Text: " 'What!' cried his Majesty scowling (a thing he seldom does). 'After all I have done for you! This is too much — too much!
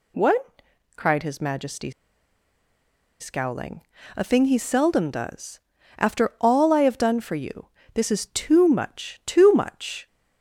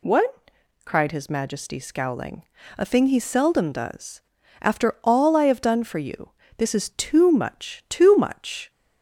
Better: second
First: pauses between "Majesty" and "scowling"; strong; at 1.9 s; 1.2 s long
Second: none

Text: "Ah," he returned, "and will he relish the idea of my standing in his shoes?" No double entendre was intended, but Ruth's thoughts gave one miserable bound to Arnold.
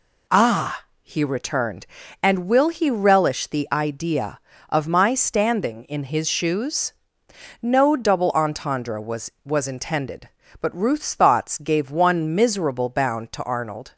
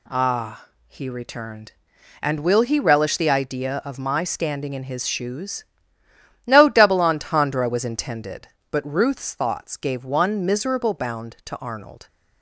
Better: second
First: says "was" twice; at 9.4 s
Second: none

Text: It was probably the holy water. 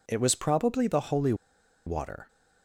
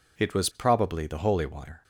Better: second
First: pauses between "holy" and "water"; noticeable; at 1.3 s; 0.52 s long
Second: none

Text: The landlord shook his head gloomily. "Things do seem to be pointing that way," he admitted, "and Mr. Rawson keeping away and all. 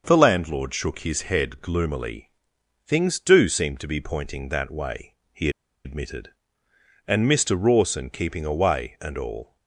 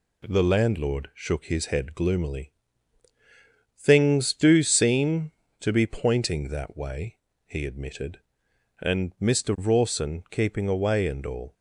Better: second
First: pauses between "he" and "admitted"; slight; at 5.4 s; 0.35 s long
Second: none

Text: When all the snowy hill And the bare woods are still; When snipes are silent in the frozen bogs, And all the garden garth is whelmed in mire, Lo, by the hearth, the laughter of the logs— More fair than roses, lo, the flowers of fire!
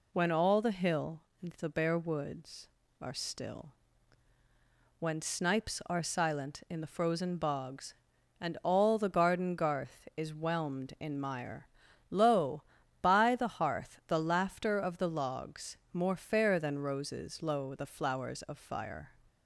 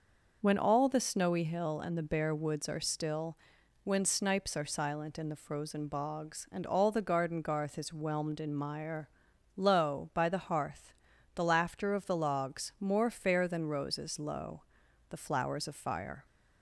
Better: second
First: skips "snowy"; at 0.7 s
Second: none

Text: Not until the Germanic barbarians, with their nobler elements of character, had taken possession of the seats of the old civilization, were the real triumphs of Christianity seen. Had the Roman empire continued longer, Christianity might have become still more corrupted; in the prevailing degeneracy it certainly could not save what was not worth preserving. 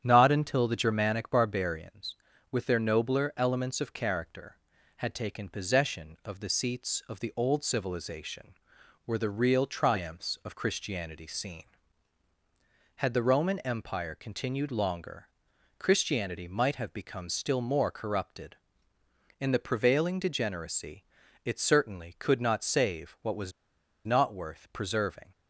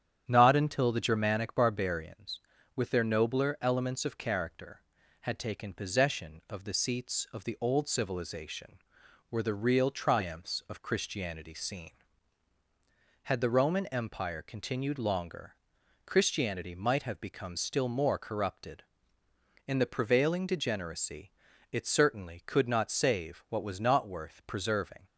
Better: second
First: starts louder than the rest; strong; until 1.0 s; 9 dB // pauses between "degeneracy" and "it"; at 21.0 s; 0.42 s long // pauses between "was" and "not"; noticeable; at 23.5 s; 0.53 s long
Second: starts louder than the rest; strong; until 1.2 s; 9 dB // pauses between "degeneracy" and "it"; at 21.2 s; 0.42 s long

